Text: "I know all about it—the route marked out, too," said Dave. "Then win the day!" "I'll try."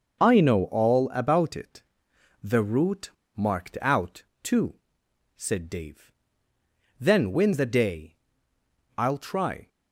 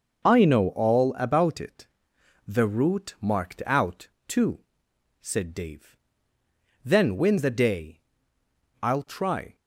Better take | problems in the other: second | pauses between "route" and "marked"; slight; at 3.1 s; 0.27 s long

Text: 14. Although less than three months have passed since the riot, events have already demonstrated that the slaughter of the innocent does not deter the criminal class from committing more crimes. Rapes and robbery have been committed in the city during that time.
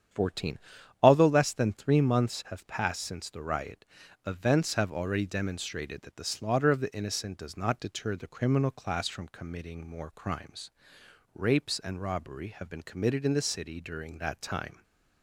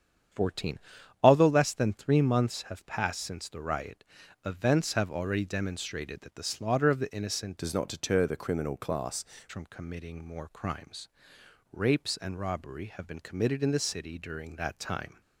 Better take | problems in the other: first | starts louder than the rest; strong; until 1.7 s; 8.5 dB; strong in the first // changes voice from "does" to "class"; from 7.5 to 9.2 s; 1.7 s long

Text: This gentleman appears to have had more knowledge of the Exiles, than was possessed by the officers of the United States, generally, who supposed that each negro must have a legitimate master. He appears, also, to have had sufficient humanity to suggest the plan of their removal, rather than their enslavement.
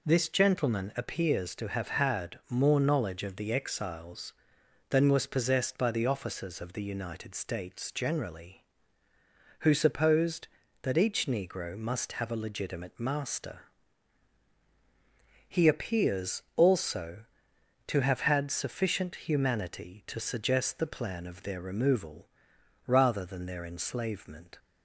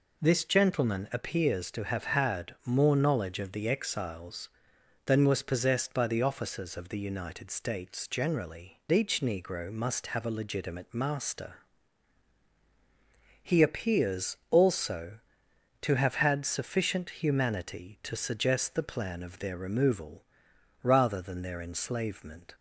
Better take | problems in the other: first | skips "who supposed that"; at 8.8 s

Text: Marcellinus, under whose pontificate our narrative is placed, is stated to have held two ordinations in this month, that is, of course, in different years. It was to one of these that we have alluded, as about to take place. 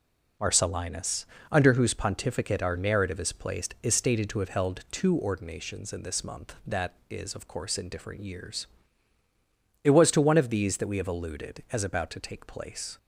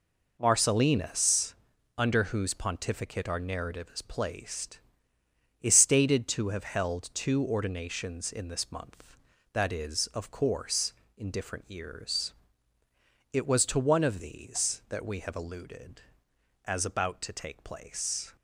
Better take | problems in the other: neither | none

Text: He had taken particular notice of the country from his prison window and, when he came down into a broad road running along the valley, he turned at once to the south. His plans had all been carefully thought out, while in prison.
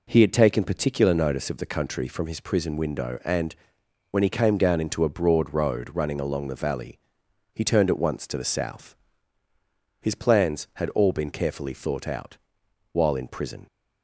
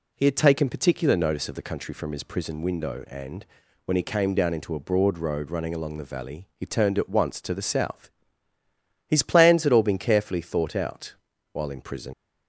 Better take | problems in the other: first | leaves "prison" unfinished; at 12.1 s; 70 ms

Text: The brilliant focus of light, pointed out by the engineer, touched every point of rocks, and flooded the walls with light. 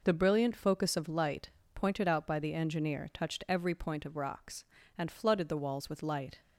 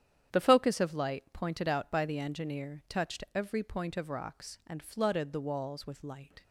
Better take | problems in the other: first | starts louder than the rest; strong; until 1.3 s; 10 dB // skips "brilliant"; at 0.4 s

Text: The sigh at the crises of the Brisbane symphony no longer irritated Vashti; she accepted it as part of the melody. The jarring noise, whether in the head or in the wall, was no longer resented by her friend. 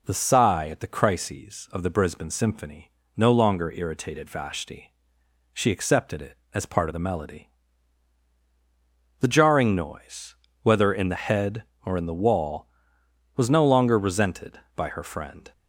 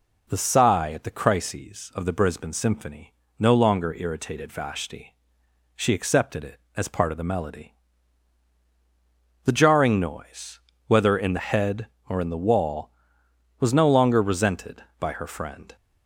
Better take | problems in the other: neither | pauses between "symphony" and "no"; slight; the same in both

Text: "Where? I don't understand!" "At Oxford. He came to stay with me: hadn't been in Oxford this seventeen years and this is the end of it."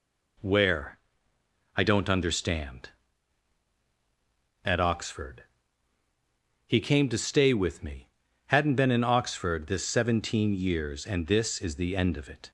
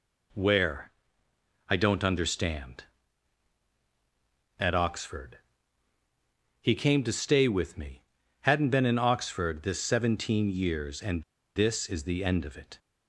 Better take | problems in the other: first | pauses between "and" and "this"; slight; at 11.2 s; 0.32 s long

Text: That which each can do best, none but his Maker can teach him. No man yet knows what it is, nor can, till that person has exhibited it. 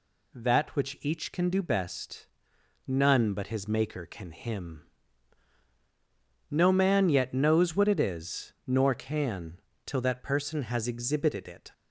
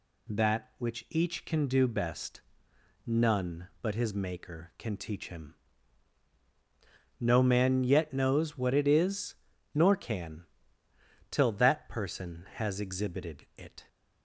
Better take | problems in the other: second | skips "teach"; at 4.3 s

